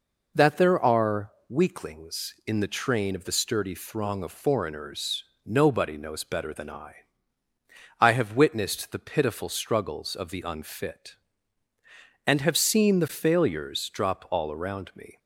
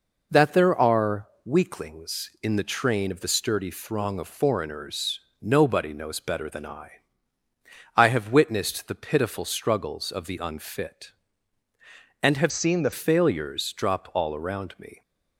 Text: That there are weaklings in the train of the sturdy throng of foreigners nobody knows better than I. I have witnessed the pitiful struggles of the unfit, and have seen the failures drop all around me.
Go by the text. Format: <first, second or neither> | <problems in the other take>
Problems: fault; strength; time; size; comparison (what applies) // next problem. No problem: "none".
first | pauses between "are" and "weaklings"; slight; at 1.2 s; 0.16 s long; slight in the first // pauses between "foreigners" and "nobody"; slight; at 5.1 s; 0.22 s long; slight in the first // changes voice from "seen" to "the"; from 12.5 to 12.9 s; 0.4 s long